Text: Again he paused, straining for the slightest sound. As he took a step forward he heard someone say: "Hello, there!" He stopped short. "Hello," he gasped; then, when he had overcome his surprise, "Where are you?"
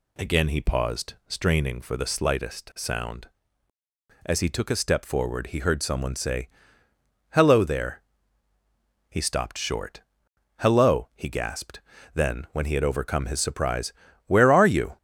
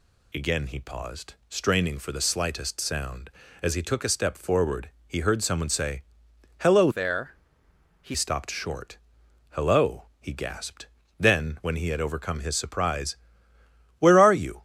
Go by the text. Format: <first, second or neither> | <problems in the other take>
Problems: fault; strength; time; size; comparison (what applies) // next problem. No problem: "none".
first | pauses between "forward" and "he"; slight; at 4.8 s; 0.18 s long // changes voice from "there" to "He"; from 6.9 to 8.1 s; 1.2 s long